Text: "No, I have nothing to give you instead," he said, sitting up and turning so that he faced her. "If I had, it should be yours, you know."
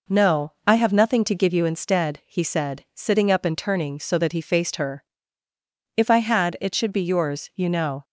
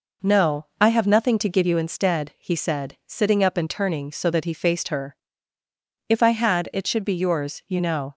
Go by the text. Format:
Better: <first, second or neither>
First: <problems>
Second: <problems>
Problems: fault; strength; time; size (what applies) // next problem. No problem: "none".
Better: neither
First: none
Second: none